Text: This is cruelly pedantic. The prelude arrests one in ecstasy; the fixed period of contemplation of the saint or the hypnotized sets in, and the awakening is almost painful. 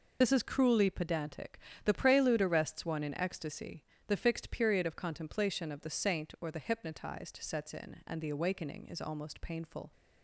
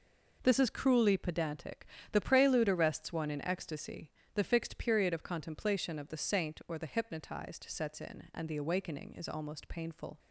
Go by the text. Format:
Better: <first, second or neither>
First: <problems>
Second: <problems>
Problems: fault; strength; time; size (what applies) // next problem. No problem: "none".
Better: second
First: loses the start of "This"; at 0.2 s; 70 ms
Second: none